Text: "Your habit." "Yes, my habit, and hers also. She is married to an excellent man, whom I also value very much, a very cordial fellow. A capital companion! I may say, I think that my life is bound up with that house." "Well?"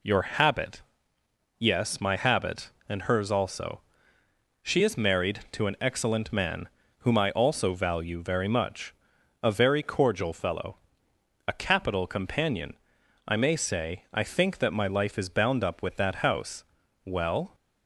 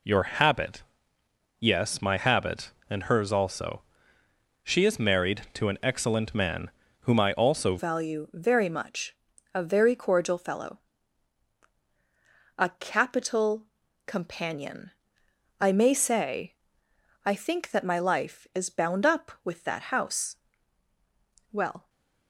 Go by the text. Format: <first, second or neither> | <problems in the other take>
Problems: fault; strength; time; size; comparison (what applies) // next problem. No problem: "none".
first | changes voice at "value"; from 7.7 s on; 14.1 s long // pauses between "capital" and "companion"; at 13.6 s; 0.38 s long // stays silent after the last word; slight; from 21.7 s on; 0.5 s long